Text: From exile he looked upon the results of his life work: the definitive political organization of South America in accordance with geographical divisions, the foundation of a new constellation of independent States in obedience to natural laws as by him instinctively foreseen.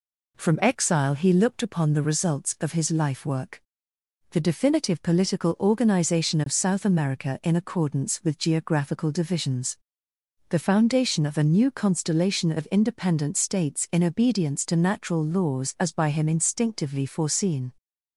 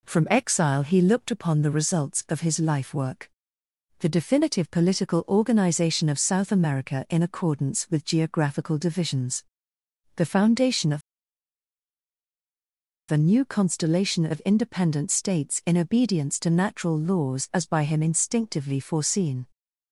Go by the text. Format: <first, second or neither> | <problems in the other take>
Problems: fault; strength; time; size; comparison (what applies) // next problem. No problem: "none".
first | pauses between "of" and "a"; strong; at 11.0 s; 2.1 s long